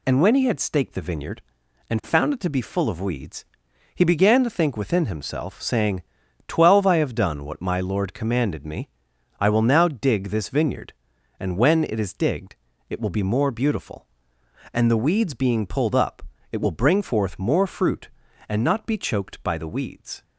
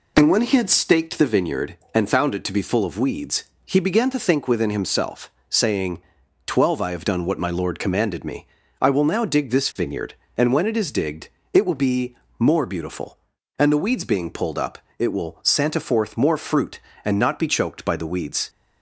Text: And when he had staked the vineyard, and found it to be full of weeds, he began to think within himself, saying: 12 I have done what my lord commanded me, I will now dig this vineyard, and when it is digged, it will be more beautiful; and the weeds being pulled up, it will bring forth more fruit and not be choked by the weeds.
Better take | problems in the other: first | pauses between "be" and "more"; slight; at 12.1 s; 0.24 s long // says "santa" for "bring"; at 15.4 s

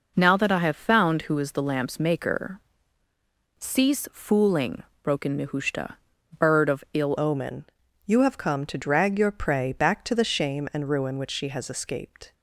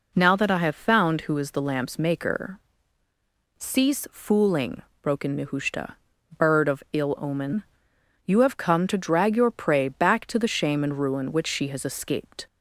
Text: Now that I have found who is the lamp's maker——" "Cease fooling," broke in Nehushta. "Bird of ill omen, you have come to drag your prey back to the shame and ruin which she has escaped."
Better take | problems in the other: second | changes voice at "omen"; from 7.1 s on; 5.2 s long

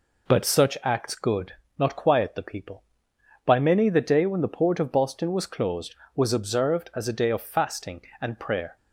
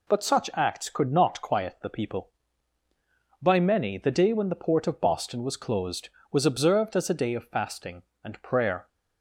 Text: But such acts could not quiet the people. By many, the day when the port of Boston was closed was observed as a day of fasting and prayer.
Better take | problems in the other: second | says "good" for "could"; at 1.1 s

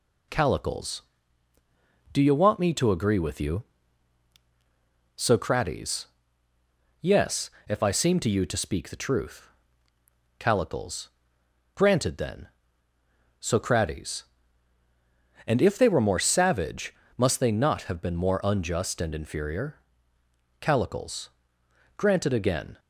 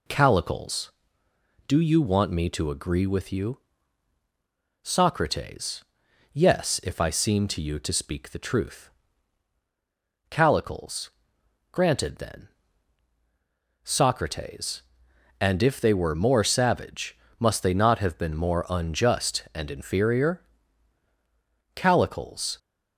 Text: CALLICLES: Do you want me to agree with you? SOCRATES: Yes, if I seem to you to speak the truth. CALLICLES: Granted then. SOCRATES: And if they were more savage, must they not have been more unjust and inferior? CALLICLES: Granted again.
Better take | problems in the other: first | stops before "Granted again"; at 22.5 s

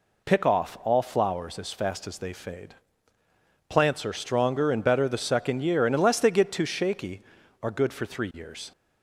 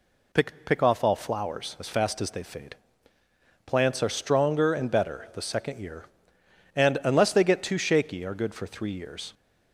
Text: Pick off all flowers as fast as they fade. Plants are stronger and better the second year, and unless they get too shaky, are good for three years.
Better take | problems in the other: first | says "Pick" twice; at 0.6 s

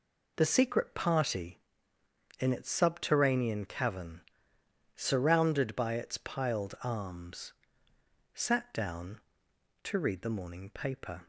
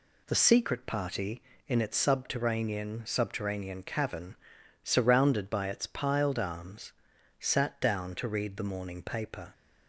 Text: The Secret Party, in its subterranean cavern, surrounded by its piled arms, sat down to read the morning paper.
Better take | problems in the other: first | says "subterranean" twice; at 3.0 s

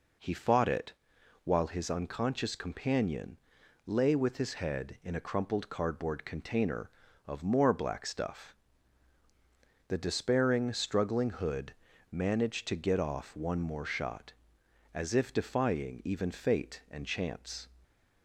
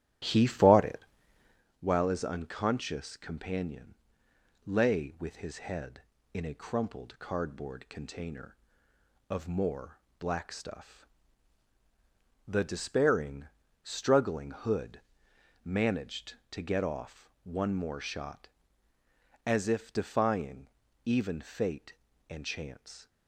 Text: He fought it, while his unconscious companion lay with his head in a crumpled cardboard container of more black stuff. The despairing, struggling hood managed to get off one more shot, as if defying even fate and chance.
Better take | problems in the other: first | starts louder than the rest; strong; until 1.6 s; 12 dB // pauses between "companion" and "lay"; noticeable; at 3.9 s; 0.70 s long; noticeable in the first // pauses between "more" and "black"; slight; at 9.9 s; 0.20 s long // pauses between "hood" and "managed"; noticeable; at 15.0 s; 0.64 s long; also in the first // pauses between "defying" and "even"; slight; at 20.6 s; 0.34 s long

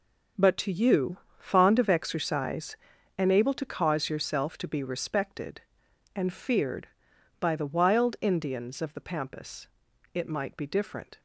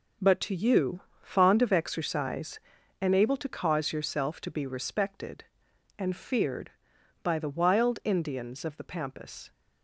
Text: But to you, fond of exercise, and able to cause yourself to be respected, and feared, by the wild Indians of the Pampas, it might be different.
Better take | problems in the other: first | stops before "it might be different"; at 9.5 s

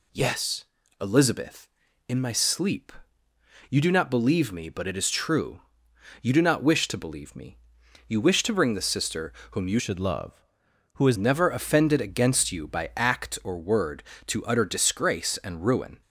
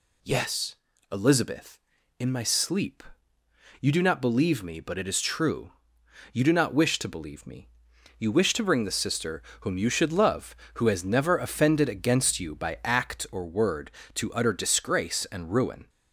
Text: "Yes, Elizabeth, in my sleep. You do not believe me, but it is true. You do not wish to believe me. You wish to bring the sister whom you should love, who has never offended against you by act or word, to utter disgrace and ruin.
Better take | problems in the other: second | pauses between "sister" and "whom"; slight; at 9.3 s; 0.20 s long; slight in the second // changes voice from "should" to "has"; from 9.7 to 11.1 s; 1.4 s long

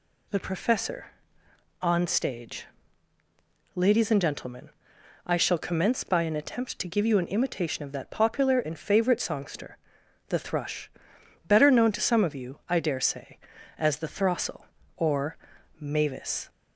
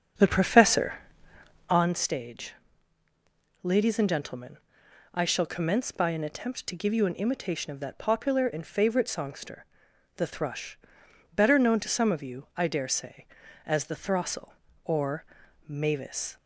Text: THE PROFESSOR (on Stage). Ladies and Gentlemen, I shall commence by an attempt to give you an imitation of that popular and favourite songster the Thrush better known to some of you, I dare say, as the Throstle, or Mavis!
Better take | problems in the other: first | starts louder than the rest; strong; until 1.9 s; 7.5 dB // pauses between "songster" and "the"; noticeable; at 9.6 s; 0.50 s long; noticeable in the first // pauses between "Thrush" and "better"; noticeable; at 10.7 s; 0.54 s long; noticeable in the first // pauses between "or" and "Mavis"; at 15.2 s; 0.42 s long; also in the first

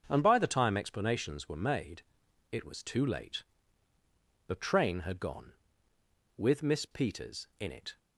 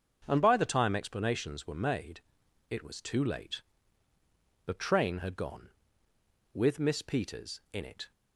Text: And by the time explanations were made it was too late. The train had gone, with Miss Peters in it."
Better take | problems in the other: neither | starts louder than the rest; the same in both // pauses between "made" and "it"; noticeable; the same in both

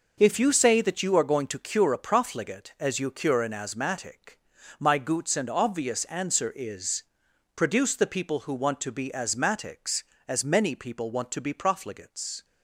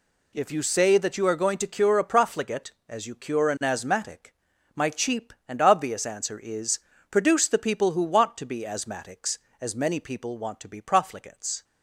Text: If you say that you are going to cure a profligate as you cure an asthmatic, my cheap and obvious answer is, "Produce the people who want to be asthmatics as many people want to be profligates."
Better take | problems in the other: second | says "goots" for "cheap"; at 4.9 s

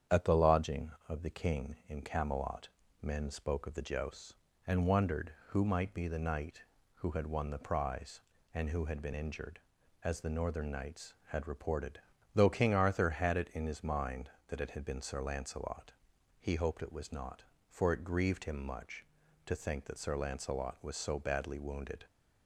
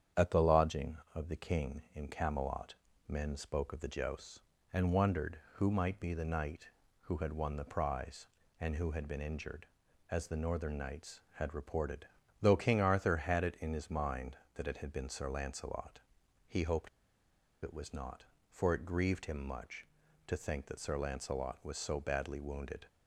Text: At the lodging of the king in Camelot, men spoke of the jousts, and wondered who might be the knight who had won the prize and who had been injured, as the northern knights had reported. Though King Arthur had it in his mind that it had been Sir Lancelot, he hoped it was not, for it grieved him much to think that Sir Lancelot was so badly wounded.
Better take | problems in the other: first | starts louder than the rest; strong; until 1.3 s; 8.5 dB; strong in the first // pauses between "hoped" and "it"; noticeable; at 16.8 s; 0.76 s long

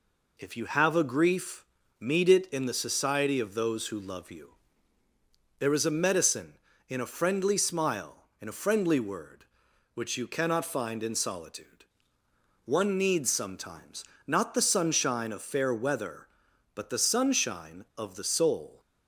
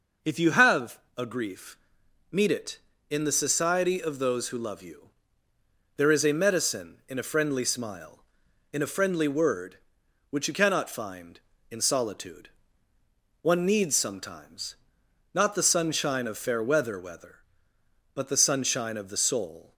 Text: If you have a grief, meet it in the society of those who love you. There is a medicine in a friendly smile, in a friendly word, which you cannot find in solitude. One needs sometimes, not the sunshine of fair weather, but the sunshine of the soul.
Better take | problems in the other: first | pauses between "have" and "a"; slight; at 0.9 s; 0.18 s long // says "weather" twice; at 16.9 s

